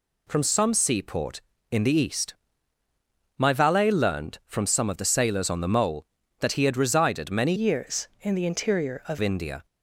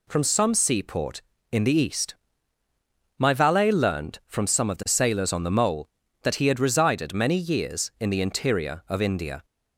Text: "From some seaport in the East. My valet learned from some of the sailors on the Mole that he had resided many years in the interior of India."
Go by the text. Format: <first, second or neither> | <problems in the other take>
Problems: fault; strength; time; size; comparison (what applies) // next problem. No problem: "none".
second | changes voice from "years" to "of"; from 7.5 to 9.1 s; 1.6 s long